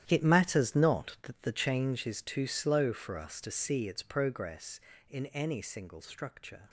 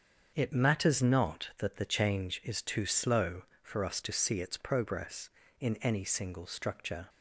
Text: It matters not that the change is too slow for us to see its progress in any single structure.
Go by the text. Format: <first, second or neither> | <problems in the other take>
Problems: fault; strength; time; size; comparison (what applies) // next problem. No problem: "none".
second | gets quieter; strong; throughout; 14 dB // starts louder than the rest; strong; until 1.0 s; 11 dB; also in the second